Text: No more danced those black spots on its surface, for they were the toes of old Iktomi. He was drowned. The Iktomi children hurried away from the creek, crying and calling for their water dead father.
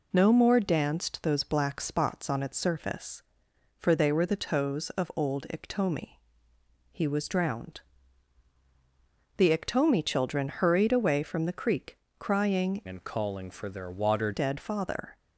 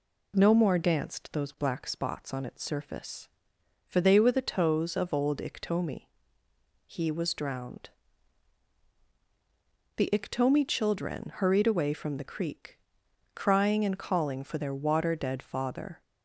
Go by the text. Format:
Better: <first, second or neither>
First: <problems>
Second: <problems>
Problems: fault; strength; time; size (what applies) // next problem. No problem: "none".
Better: second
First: changes voice from "and" to "water"; from 12.8 to 14.2 s; 1.4 s long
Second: none